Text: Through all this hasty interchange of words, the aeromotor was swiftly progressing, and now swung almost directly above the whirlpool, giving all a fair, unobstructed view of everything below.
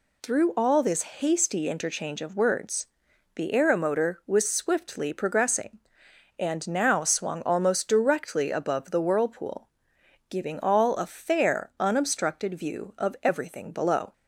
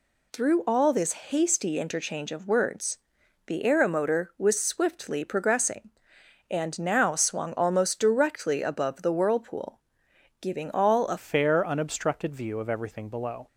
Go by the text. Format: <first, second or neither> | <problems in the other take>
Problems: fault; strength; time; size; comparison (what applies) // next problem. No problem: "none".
first | changes voice at "fair"; from 11.1 s on; 2.3 s long